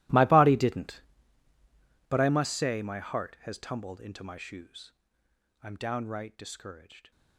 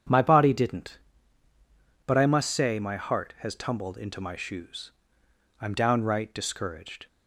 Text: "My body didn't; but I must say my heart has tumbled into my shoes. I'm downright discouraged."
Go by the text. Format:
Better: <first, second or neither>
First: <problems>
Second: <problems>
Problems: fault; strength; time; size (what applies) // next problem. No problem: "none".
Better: second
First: gets quieter; strong; throughout; 20.5 dB // starts louder than the rest; strong; until 2.1 s; 16.5 dB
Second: starts louder than the rest; strong; until 2.1 s; 8 dB